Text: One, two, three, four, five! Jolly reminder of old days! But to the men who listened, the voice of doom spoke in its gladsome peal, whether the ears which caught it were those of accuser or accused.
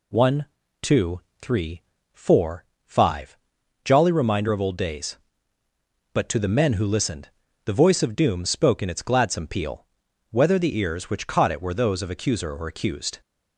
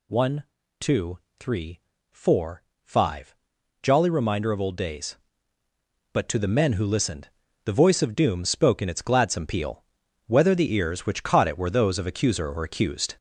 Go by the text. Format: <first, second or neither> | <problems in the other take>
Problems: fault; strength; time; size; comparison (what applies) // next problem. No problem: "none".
first | gets louder; throughout; 6 dB